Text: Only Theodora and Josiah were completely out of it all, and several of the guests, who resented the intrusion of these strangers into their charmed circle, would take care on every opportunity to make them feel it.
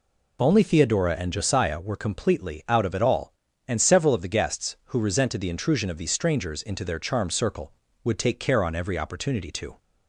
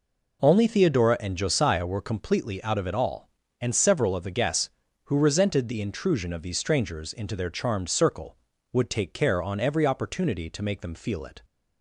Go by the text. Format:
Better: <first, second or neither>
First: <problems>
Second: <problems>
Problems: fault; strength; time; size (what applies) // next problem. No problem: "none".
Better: second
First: stops before "make them feel it"; at 9.8 s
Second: none